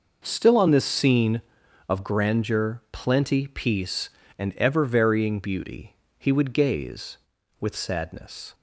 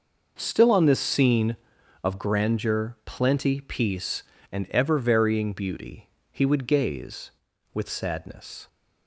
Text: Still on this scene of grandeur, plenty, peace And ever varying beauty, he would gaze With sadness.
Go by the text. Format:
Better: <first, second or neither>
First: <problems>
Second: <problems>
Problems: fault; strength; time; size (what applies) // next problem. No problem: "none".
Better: neither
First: none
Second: none